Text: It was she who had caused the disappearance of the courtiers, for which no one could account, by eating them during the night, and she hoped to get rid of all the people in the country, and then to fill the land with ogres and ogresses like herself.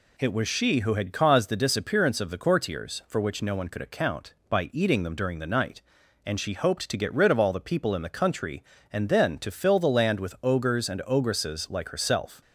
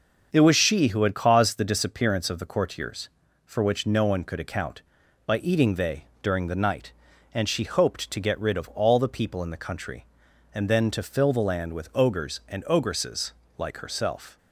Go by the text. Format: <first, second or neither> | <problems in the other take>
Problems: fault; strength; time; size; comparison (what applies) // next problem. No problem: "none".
first | starts louder than the rest; until 1.3 s; 6 dB // says "they" for "them"; at 5.7 s // pauses between "ogresses" and "like"; slight; at 13.3 s; 0.24 s long